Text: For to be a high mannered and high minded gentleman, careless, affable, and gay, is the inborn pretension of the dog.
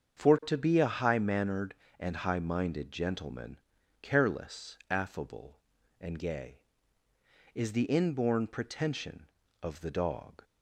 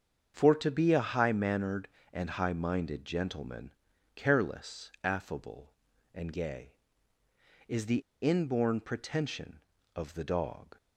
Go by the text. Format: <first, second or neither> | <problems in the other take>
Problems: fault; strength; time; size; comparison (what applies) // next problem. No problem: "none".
first | starts louder than the rest; strong; until 1.3 s; 7 dB; also in the first // pauses between "the" and "inborn"; slight; at 8.0 s; 0.20 s long